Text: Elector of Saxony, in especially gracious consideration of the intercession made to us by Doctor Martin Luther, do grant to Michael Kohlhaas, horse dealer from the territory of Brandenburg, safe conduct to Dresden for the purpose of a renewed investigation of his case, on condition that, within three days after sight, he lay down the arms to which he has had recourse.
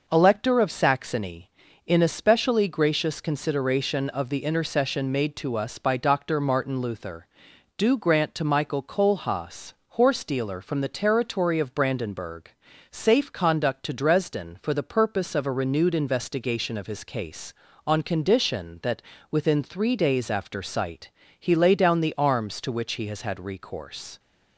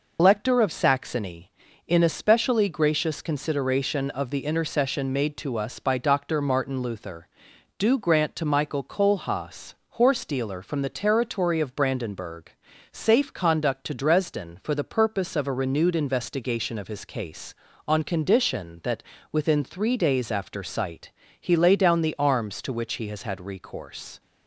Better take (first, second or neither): first